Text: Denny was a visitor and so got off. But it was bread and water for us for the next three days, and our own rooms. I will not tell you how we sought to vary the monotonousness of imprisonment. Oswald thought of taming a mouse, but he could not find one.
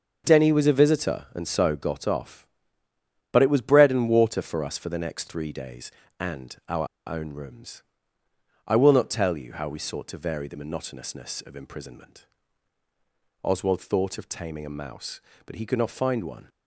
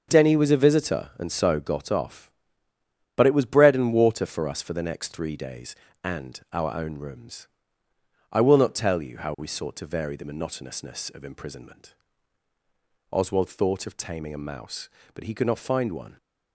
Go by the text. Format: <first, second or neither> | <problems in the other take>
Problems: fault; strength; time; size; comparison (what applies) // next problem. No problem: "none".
second | starts louder than the rest; until 1.2 s; 6.5 dB; also in the second // pauses between "our" and "own"; slight; at 6.8 s; 0.21 s long